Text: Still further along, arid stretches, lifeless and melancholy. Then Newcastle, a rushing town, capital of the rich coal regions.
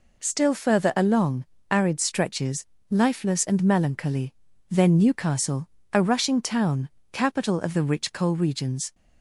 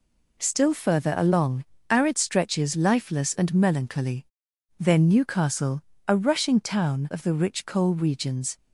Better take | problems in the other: first | skips "capital"; at 7.1 s

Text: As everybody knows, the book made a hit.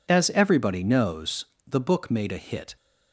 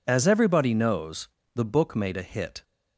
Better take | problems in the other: neither | none

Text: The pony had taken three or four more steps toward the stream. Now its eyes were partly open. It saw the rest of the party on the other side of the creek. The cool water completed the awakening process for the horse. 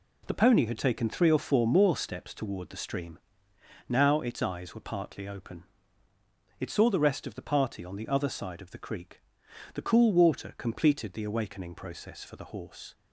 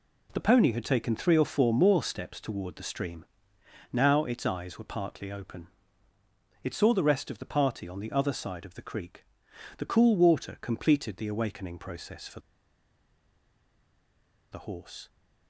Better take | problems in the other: first | pauses between "for" and "the"; strong; at 12.3 s; 2.1 s long

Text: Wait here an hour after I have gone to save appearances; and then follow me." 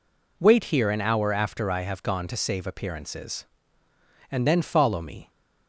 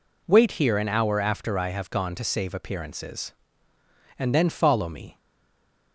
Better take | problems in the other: first | stays silent after the last word; slight; from 5.1 s on; 0.8 s long

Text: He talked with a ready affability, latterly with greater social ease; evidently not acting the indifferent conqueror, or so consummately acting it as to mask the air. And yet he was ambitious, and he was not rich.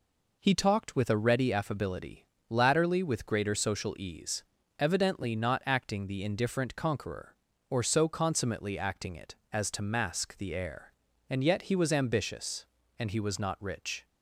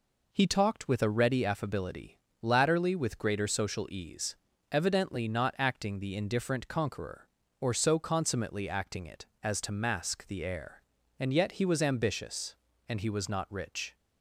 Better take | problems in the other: neither | none

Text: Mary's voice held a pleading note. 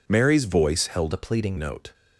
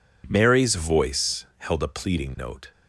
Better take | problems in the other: second | changes voice from "a" to "pleading"; from 1.1 to 1.5 s; 0.4 s long

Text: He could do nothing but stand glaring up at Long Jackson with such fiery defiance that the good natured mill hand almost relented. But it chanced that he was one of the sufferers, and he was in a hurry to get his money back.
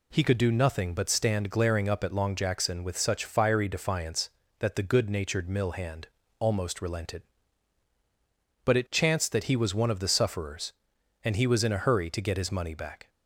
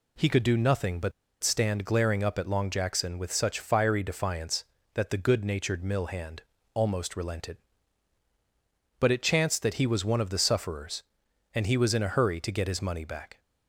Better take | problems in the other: first | pauses between "but" and "stand"; slight; at 1.1 s; 0.30 s long // pauses between "hand" and "almost"; slight; at 6.4 s; 0.30 s long; slight in the first

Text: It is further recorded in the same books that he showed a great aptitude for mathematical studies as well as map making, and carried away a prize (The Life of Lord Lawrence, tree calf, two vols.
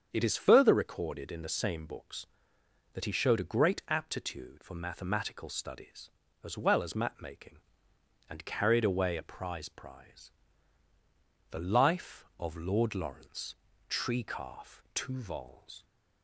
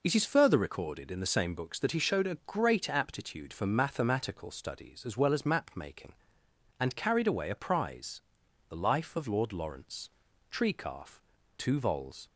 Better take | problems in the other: second | starts louder than the rest; strong; until 1.1 s; 7.5 dB // says "prize" twice; at 9.6 s

